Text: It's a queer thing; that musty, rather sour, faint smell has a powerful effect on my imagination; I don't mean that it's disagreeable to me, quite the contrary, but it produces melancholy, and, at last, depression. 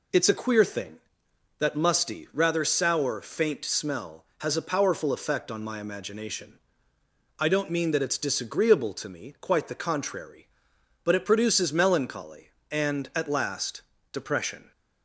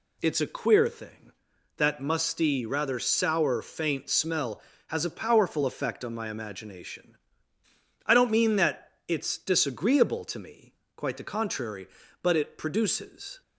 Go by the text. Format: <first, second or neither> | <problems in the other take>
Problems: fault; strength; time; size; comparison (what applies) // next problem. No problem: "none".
first | stops before "melancholy and at last depression"; at 13.4 s